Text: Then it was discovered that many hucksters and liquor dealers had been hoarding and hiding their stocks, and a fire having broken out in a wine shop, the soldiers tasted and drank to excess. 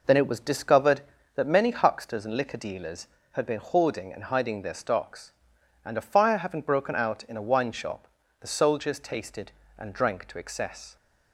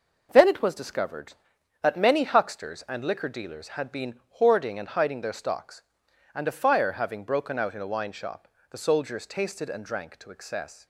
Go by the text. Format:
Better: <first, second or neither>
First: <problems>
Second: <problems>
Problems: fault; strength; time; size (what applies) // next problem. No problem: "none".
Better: neither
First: none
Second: none